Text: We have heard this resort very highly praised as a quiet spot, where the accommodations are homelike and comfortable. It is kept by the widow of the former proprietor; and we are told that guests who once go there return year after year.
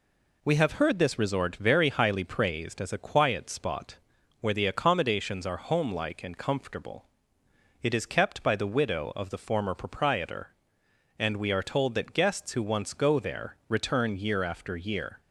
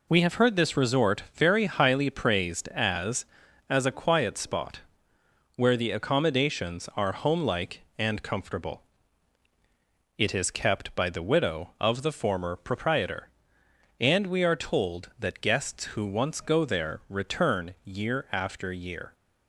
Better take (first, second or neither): first